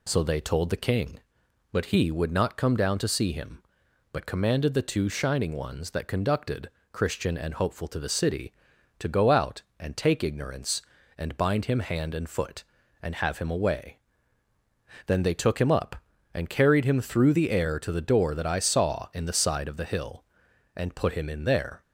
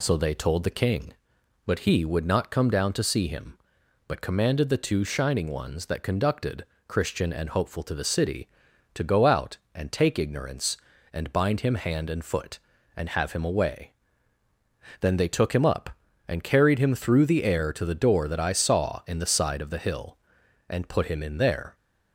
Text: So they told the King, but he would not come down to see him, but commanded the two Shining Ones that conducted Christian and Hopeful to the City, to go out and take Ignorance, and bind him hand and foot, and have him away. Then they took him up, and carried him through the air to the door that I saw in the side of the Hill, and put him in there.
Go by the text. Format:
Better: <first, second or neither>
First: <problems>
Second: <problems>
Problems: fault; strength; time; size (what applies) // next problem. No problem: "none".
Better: neither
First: pauses between "conducted" and "Christian"; slight; at 6.6 s; 0.22 s long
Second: pauses between "conducted" and "Christian"; slight; at 6.6 s; 0.22 s long